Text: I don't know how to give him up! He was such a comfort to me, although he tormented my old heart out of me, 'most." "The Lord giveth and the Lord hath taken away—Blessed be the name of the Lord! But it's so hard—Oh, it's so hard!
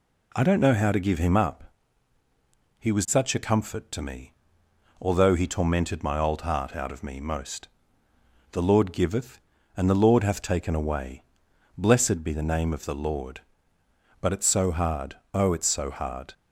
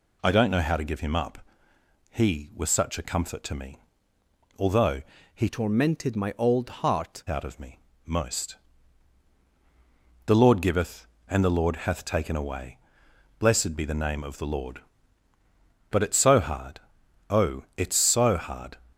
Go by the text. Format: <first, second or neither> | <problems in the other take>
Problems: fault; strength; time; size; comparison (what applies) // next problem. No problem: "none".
first | pauses between "although" and "he"; slight; at 5.0 s; 0.32 s long // changes voice from "tormented" to "heart"; from 5.4 to 7.2 s; 1.8 s long